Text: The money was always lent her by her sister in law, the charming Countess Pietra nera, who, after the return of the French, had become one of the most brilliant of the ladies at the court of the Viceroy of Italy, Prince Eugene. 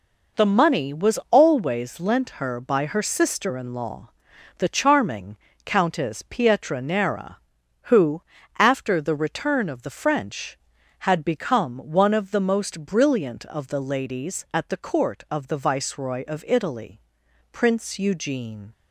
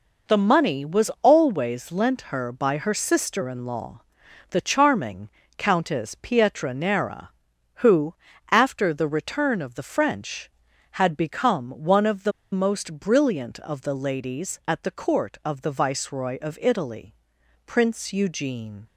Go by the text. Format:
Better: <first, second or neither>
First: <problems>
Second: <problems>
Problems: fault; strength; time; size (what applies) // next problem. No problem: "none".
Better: first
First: pauses between "charming" and "Countess"; slight; at 5.3 s; 0.26 s long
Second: pauses between "charming" and "Countess"; slight; at 5.2 s; 0.26 s long // pauses between "the" and "most"; slight; at 12.3 s; 0.22 s long